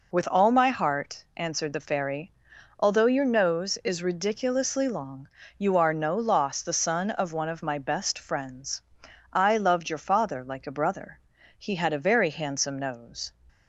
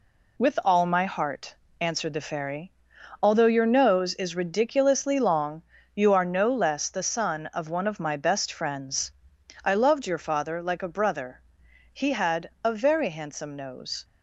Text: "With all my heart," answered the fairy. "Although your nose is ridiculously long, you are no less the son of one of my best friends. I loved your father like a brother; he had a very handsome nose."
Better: second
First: says "loss" for "less"; at 6.1 s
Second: none

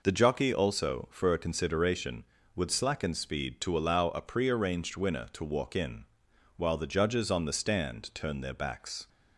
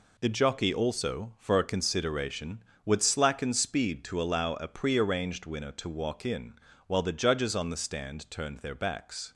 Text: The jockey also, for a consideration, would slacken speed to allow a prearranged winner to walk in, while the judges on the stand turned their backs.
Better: neither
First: none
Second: none

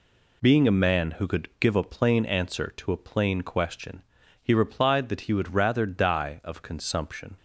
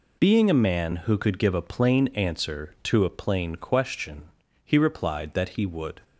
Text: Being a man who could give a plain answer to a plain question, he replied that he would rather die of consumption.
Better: first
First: none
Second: stops before "rather die of consumption"; at 6.0 s

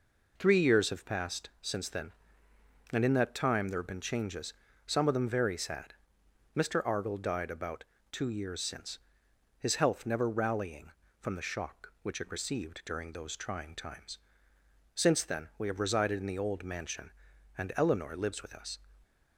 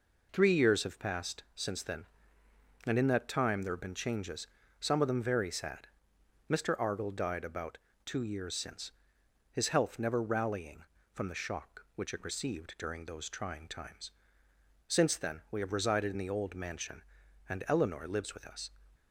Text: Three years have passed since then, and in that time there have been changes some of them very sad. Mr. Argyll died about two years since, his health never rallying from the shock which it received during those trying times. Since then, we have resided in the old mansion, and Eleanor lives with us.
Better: neither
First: pauses between "changes" and "some"; slight; at 4.5 s; 0.34 s long // pauses between "about" and "two"; slight; at 7.8 s; 0.28 s long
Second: pauses between "changes" and "some"; slight; at 4.4 s; 0.34 s long // pauses between "about" and "two"; slight; at 7.7 s; 0.28 s long

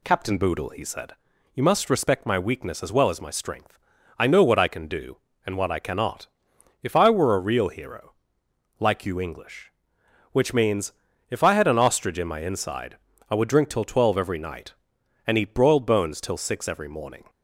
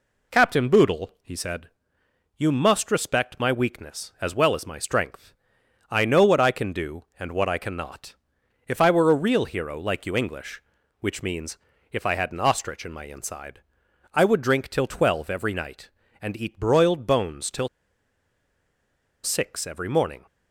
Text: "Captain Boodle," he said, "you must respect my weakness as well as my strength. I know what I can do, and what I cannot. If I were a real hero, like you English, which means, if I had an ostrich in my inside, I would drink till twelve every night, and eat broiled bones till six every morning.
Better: first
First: none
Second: pauses between "till" and "six"; strong; at 17.6 s; 1.5 s long

